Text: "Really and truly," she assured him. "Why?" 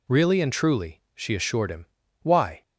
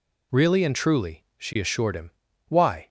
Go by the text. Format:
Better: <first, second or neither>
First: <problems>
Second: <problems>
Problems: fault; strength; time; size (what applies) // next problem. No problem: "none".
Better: neither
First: none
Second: none